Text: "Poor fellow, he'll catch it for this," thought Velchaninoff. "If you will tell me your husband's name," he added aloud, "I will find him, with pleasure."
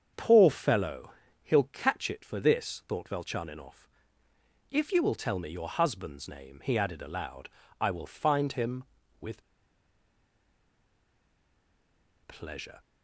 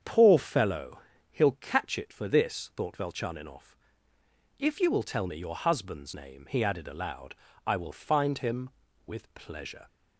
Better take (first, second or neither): second